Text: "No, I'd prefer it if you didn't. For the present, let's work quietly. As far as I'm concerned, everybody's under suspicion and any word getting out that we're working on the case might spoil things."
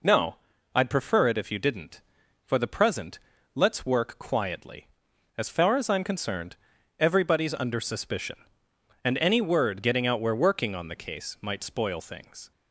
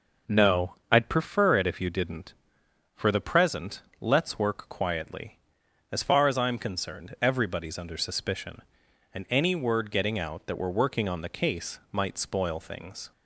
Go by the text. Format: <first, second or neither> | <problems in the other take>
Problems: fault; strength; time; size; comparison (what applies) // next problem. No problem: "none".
second | skips "that"; at 10.2 s